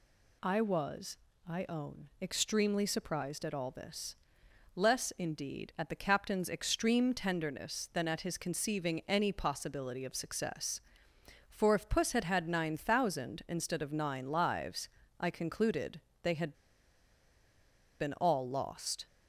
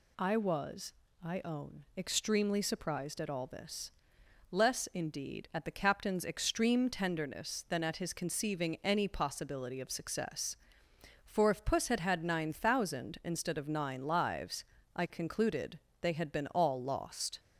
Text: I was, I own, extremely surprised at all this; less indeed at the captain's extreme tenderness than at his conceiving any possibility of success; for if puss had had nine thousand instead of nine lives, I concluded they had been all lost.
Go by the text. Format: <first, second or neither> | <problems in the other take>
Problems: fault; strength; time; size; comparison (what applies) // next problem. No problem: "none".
second | pauses between "concluded" and "they"; slight; at 15.9 s; 0.24 s long; slight in the second // pauses between "had" and "been"; strong; at 16.5 s; 1.4 s long